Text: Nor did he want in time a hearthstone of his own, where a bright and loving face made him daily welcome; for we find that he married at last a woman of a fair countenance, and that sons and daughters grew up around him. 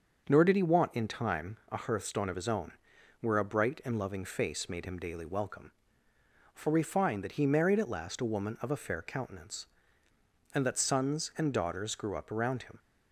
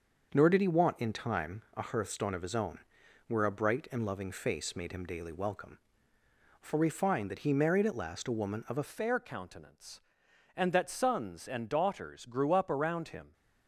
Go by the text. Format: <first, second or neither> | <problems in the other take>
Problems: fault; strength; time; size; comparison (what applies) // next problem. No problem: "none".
first | starts louder than the rest; until 1.3 s; 6 dB; also in the first // changes voice at "fair"; from 8.8 s on; 4.5 s long